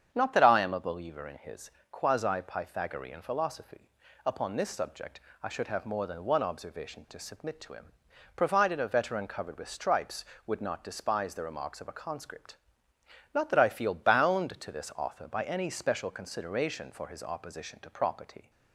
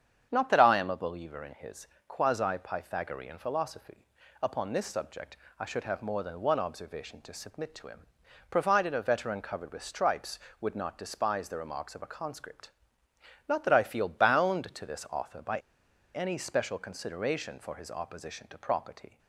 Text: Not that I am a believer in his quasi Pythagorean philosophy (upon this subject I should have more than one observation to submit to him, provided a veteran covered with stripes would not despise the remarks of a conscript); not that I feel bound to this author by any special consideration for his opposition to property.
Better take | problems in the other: first | starts louder than the rest; strong; until 1.3 s; 8 dB; strong in the first // pauses between "his" and "quasi"; slight; at 1.8 s; 0.22 s long; slight in the first // pauses between "subject" and "I"; slight; at 5.3 s; 0.20 s long; slight in the first // pauses between "by" and "any"; noticeable; at 15.5 s; 0.56 s long

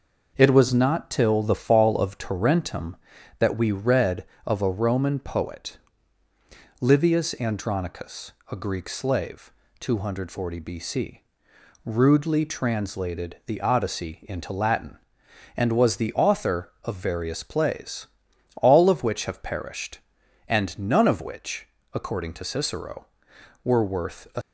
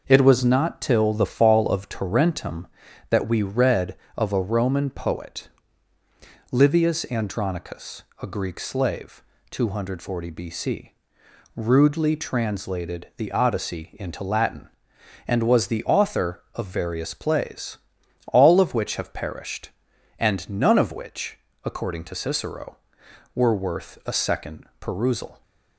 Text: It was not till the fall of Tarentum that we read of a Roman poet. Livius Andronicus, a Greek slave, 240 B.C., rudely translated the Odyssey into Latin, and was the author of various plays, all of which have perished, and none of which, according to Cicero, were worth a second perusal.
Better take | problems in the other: second | stops before "second perusal"; at 24.4 s

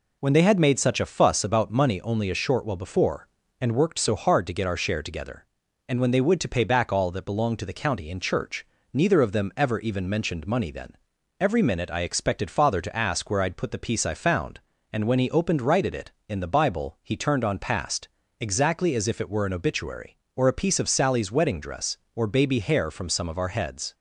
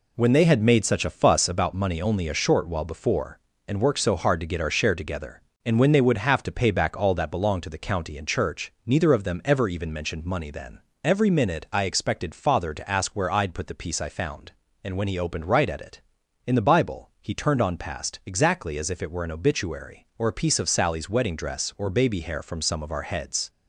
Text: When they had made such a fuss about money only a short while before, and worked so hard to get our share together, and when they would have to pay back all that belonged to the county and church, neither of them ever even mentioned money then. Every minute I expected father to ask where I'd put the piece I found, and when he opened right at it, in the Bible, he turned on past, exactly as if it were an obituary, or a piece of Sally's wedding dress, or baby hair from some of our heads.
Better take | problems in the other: second | skips "have"; at 6.3 s

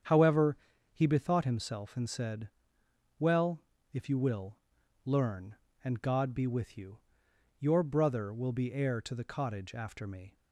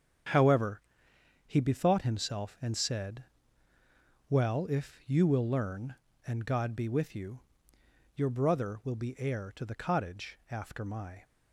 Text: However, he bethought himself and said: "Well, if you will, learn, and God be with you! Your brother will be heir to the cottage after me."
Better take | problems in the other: first | starts louder than the rest; strong; until 1.9 s; 8 dB; strong in the first // says "my" for "me"; at 10.8 s

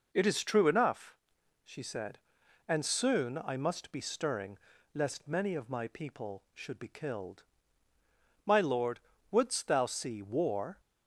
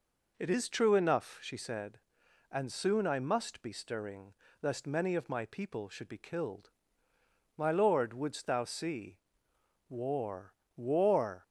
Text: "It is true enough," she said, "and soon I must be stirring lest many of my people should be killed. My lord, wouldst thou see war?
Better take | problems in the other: first | pauses between "stirring" and "lest"; slight; at 4.3 s; 0.28 s long; slight in the first // pauses between "see" and "war"; noticeable; at 9.1 s; 0.70 s long // says "war" twice; at 10.7 s

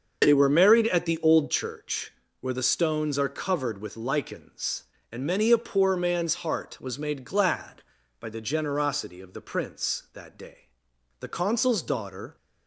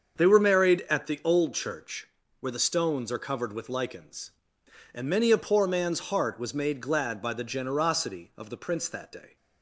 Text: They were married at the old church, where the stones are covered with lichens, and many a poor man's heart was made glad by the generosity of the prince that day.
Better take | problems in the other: second | starts louder than the rest; until 1.2 s; 6 dB; also in the second // goes on to say "The consul's daughter"; noticeable; from 11.1 s on; 1.1 s long

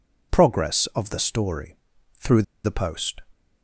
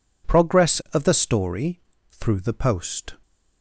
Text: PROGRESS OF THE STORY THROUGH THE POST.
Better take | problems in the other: second | pauses between "STORY" and "THROUGH"; noticeable; at 1.7 s; 0.46 s long; slight in the second // pauses between "THROUGH" and "THE"; slight; at 2.4 s; 0.21 s long

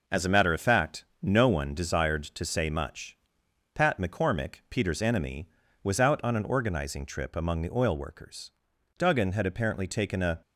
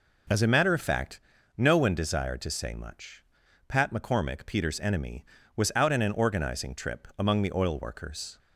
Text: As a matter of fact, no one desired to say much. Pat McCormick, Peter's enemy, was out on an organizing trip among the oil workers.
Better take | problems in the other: second | goes on to say "Duggan had apparently taken a"; from 8.9 s on; 1.4 s long

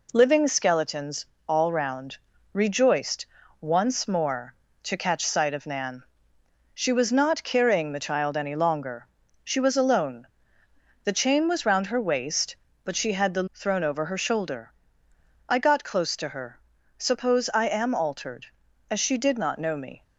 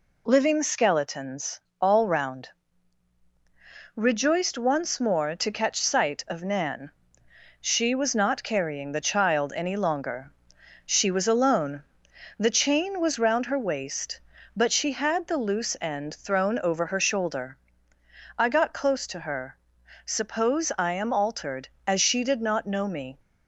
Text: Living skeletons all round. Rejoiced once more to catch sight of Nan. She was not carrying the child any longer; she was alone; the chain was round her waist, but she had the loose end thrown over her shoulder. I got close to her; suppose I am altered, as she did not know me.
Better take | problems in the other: second | pauses between "skeletons" and "all"; slight; at 1.2 s; 0.24 s long; slight in the second // pauses between "Rejoiced" and "once"; slight; at 3.2 s; 0.36 s long // skips "loose end"; at 13.5 s

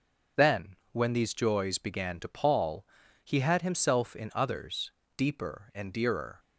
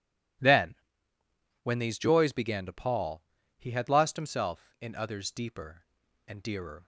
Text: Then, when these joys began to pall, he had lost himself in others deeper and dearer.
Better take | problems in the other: second | skips "lost"; at 3.6 s // pauses between "others" and "deeper"; slight; at 4.9 s; 0.26 s long

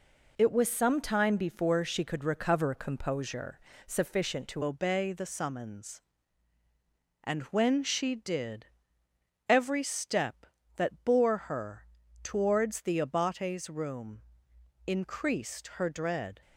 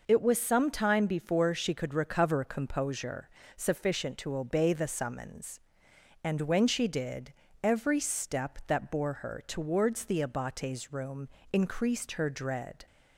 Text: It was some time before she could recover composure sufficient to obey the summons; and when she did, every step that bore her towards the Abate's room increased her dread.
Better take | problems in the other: second | pauses between "composure" and "sufficient"; slight; at 3.5 s; 0.26 s long; slight in the second // changes voice at "obey"; from 4.6 s on; 11.7 s long // pauses between "her" and "towards"; at 11.8 s; 0.38 s long // pauses between "room" and "increased"; noticeable; at 14.2 s; 0.64 s long; slight in the second

